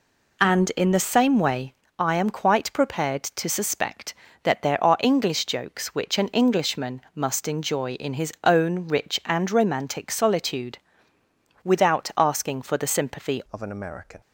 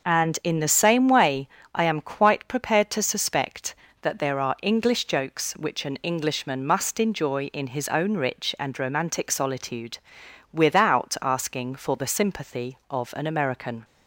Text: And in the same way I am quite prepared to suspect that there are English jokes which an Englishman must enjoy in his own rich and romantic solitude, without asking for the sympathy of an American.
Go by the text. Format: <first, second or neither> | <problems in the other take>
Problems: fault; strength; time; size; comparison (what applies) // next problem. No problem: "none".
second | pauses between "way" and "I"; slight; at 1.7 s; 0.24 s long; slight in the second // changes voice at "of"; from 13.5 s on; 0.7 s long